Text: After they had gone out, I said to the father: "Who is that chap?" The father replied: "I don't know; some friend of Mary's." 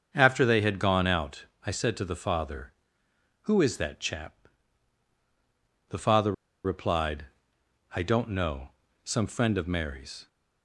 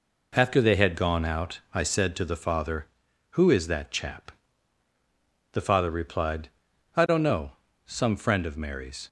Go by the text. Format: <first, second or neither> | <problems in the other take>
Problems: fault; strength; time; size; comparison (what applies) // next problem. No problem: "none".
second | starts louder than the rest; until 1.1 s; 7 dB // pauses between "father" and "replied"; slight; at 6.3 s; 0.32 s long